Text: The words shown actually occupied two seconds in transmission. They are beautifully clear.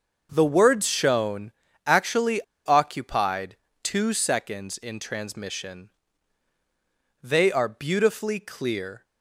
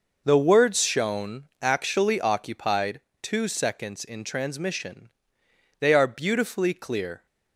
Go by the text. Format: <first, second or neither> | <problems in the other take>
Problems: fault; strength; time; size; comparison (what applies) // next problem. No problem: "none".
second | starts louder than the rest; until 1.3 s; 6.5 dB // pauses between "shown" and "actually"; slight; at 1.5 s; 0.36 s long // pauses between "actually" and "occupied"; slight; at 2.3 s; 0.26 s long // pauses between "occupied" and "two"; slight; at 3.5 s; 0.28 s long; slight in the second